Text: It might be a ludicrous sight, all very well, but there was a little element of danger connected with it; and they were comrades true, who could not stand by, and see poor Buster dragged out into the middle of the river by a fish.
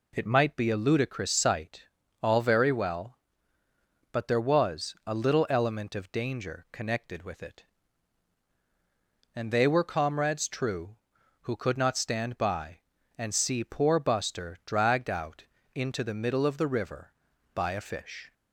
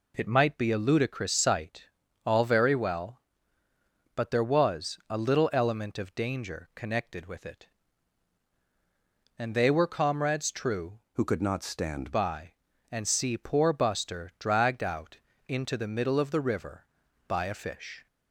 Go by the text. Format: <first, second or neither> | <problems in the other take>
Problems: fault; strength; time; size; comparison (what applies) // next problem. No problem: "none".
first | changes voice from "who" to "stand"; from 11.1 to 12.1 s; 1.0 s long // pauses between "out" and "into"; slight; at 15.1 s; 0.30 s long; slight in the first